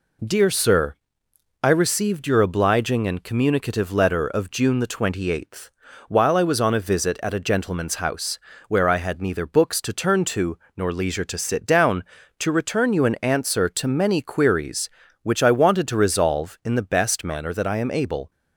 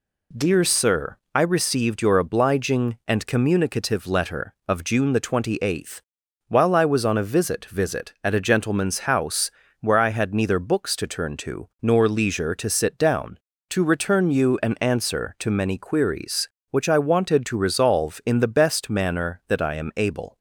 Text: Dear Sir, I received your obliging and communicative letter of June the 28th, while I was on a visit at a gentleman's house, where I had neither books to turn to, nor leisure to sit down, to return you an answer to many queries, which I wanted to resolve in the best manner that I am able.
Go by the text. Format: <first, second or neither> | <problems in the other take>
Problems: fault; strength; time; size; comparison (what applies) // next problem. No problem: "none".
first | says "visit" twice; at 7.6 s